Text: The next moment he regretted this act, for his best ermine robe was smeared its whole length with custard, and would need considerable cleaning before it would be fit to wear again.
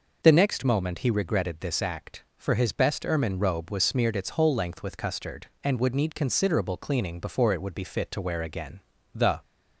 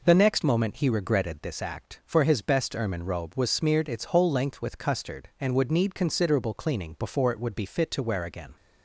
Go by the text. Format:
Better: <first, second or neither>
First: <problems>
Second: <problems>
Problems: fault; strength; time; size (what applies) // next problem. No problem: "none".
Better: second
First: goes on to say "The"; slight; from 9.1 s on; 0.28 s long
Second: none